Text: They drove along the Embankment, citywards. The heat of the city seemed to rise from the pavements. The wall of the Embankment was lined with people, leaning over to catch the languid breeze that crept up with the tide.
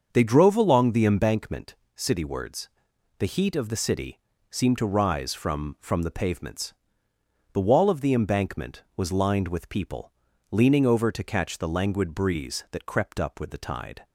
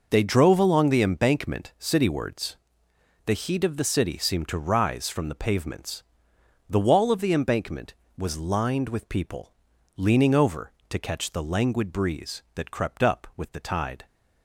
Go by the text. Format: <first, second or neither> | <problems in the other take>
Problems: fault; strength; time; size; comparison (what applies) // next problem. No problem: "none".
second | starts louder than the rest; until 1.1 s; 6.5 dB // pauses between "city" and "seemed"; slight; at 4.1 s; 0.30 s long // says "from" twice; at 5.7 s